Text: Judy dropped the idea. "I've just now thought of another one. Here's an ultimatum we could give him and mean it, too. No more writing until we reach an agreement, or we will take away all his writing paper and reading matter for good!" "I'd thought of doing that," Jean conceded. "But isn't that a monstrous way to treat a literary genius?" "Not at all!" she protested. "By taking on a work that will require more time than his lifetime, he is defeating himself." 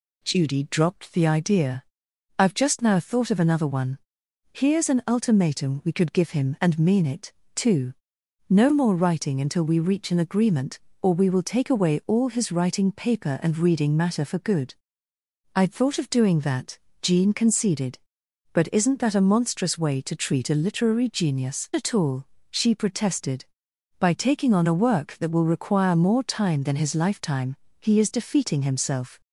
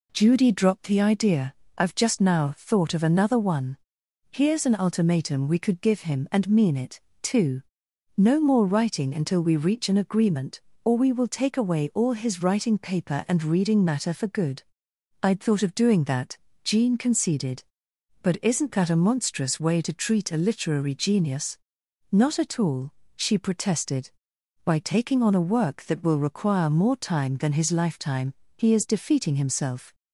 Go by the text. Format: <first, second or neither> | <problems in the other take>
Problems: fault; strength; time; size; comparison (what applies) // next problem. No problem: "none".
second | skips "Not"; at 21.7 s